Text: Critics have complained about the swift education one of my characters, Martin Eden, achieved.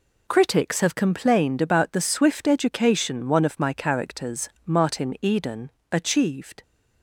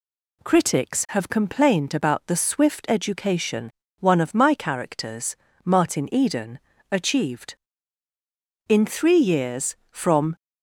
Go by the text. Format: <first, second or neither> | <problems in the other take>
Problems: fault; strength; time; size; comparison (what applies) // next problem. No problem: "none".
first | pauses between "education" and "one"; slight; at 3.6 s; 0.32 s long // goes on to say "In three years from"; strong; from 8.6 s on; 1.6 s long